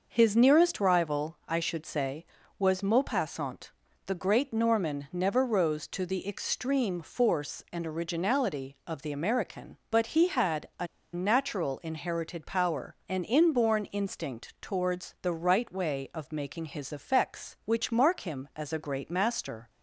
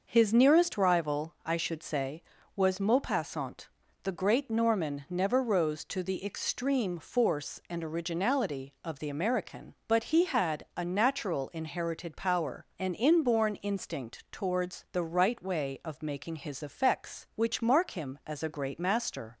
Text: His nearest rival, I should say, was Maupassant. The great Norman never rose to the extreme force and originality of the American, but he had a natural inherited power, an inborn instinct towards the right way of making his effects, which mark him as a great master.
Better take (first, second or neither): second